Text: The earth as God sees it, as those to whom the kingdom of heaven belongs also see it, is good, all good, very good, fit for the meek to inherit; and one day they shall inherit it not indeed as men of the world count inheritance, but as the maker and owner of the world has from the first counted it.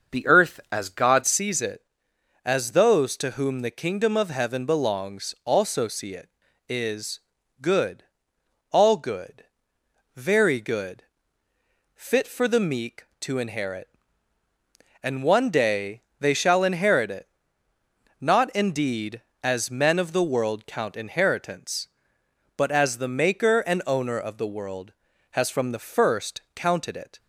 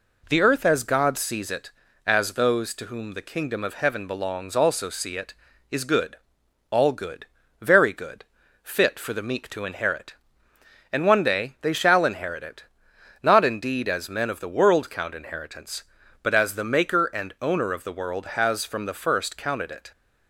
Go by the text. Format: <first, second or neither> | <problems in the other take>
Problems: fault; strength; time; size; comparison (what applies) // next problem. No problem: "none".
second | starts louder than the rest; until 1.2 s; 6.5 dB // changes voice at "sees"; from 1.2 s on; 25.9 s long // pauses between "is" and "good"; at 7.2 s; 0.40 s long // pauses between "day" and "they"; slight; at 16.0 s; 0.20 s long // pauses between "it" and "not"; noticeable; at 17.2 s; 0.94 s long; noticeable in the second